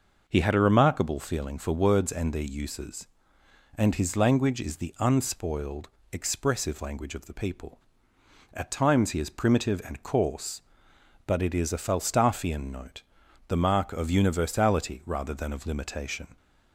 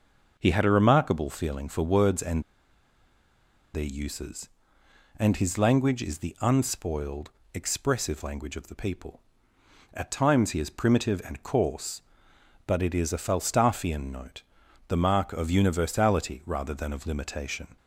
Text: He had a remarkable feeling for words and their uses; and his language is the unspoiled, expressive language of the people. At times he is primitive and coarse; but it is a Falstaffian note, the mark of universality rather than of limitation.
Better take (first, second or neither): first